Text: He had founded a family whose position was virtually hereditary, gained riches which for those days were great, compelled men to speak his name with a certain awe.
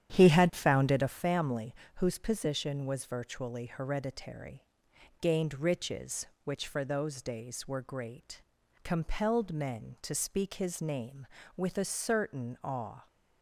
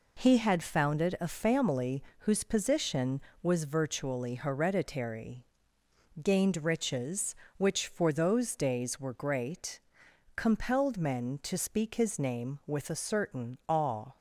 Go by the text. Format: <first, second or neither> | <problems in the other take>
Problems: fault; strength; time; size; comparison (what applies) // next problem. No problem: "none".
second | starts louder than the rest; strong; until 1.2 s; 10 dB // pauses between "family" and "whose"; slight; at 1.7 s; 0.22 s long; slight in the second